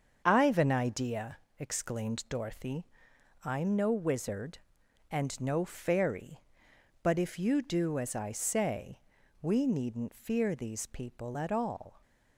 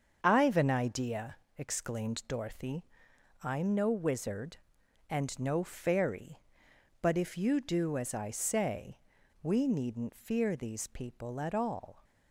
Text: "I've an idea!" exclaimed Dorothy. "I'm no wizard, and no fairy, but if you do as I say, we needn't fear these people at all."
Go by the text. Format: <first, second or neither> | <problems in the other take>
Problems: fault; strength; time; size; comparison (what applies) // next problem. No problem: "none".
neither | starts louder than the rest; the same in both